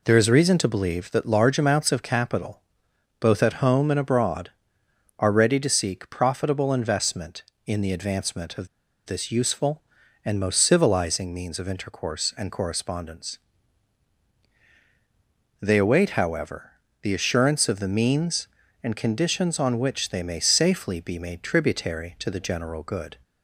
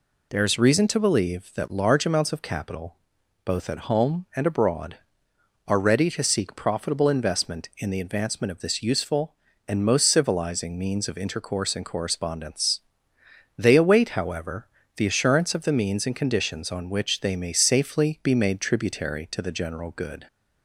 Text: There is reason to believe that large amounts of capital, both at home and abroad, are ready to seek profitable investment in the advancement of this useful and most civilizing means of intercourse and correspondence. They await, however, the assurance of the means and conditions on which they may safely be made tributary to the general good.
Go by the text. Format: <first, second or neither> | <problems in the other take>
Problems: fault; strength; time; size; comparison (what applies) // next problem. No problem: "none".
second | pauses between "of" and "this"; at 8.6 s; 0.38 s long